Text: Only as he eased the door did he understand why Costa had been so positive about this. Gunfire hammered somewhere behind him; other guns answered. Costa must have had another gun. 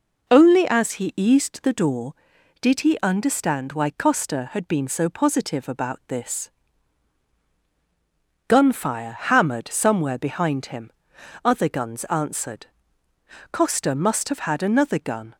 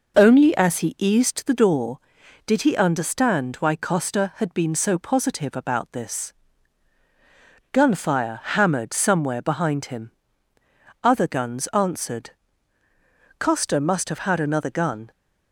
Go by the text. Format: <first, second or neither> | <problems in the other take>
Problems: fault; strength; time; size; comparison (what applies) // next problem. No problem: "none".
neither | none